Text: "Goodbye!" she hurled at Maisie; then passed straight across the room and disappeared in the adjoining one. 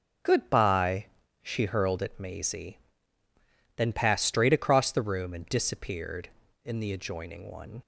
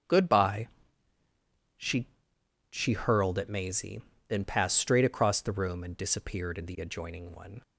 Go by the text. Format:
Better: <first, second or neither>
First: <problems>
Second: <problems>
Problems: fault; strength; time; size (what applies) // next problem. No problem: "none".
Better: first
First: starts louder than the rest; until 1.5 s; 6.5 dB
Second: starts louder than the rest; strong; until 2.7 s; 8 dB // says "she" twice; at 2.6 s